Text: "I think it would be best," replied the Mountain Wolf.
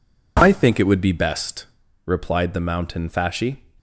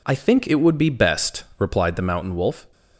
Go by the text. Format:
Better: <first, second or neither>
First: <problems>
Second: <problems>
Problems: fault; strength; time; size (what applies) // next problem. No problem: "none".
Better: second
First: says "Fasci" for "Wolf"; at 3.0 s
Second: none